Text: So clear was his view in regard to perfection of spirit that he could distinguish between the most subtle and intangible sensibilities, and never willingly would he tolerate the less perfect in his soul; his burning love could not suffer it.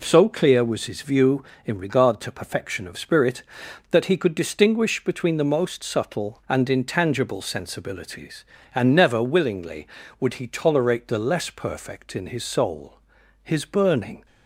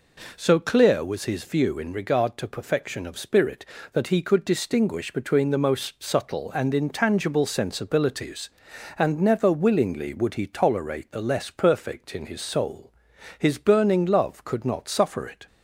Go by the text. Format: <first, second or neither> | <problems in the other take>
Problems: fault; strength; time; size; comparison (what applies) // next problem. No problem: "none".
second | stops before "love could not suffer it"; at 14.2 s